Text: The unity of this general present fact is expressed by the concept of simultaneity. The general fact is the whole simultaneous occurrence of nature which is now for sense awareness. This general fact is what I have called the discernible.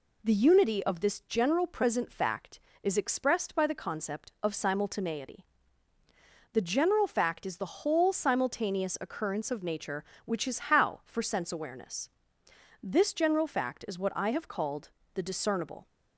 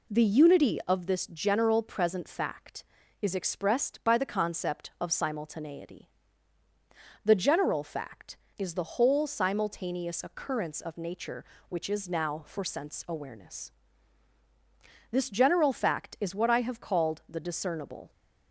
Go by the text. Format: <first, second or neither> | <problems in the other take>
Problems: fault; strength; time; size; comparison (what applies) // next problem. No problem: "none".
second | says "how" for "now"; at 10.7 s // pauses between "called" and "the"; slight; at 14.9 s; 0.24 s long